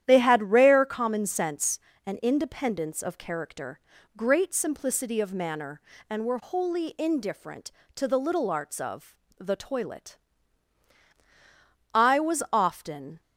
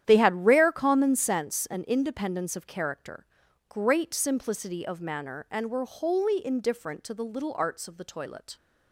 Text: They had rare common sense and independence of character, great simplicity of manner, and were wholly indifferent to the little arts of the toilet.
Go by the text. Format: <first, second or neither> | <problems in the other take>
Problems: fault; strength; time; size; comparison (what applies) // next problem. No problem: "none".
second | starts louder than the rest; strong; until 1.0 s; 11 dB; strong in the second // pauses between "of" and "the"; slight; at 9.1 s; 0.22 s long // goes on to say "I was often"; noticeable; from 11.9 s on; 1.2 s long